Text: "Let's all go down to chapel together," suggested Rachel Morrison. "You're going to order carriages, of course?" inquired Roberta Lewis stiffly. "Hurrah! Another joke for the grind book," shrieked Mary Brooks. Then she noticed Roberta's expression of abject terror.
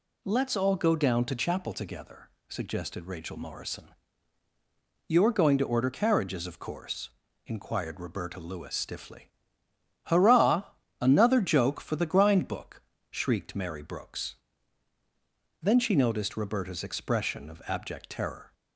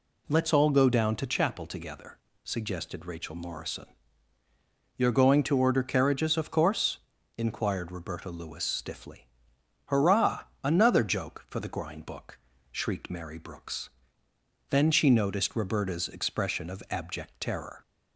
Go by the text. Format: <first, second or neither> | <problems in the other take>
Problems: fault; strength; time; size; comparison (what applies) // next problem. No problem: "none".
neither | none